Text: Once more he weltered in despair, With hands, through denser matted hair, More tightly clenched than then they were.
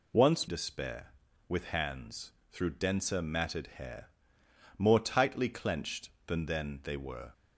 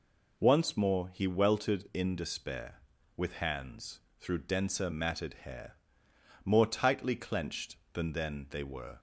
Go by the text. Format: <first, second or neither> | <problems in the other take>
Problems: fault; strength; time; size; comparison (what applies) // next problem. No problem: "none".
second | skips "more he weltered in"; at 0.4 s